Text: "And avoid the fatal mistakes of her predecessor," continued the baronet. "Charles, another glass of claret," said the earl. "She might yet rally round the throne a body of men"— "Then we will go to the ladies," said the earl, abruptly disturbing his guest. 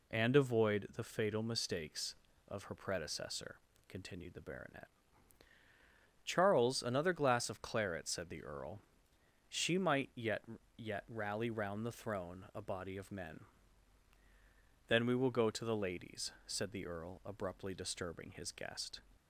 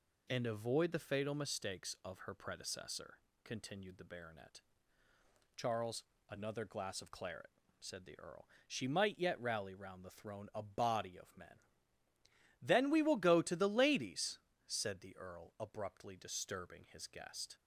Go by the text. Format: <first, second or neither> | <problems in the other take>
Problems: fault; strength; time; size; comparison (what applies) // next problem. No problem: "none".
second | says "yet" twice; at 10.7 s